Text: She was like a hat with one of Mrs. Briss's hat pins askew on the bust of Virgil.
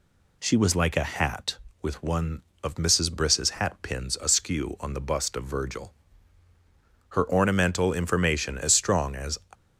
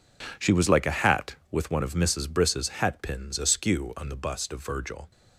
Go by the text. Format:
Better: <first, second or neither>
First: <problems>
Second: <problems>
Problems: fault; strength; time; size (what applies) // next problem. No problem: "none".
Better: second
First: goes on to say "Her ornamental information as strong as"; strong; from 7.0 s on; 2.2 s long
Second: none